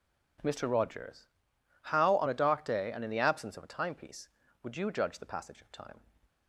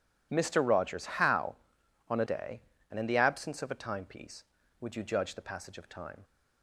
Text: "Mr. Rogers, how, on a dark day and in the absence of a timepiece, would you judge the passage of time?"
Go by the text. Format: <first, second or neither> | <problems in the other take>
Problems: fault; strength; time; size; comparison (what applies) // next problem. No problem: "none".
first | skips "dark"; at 2.2 s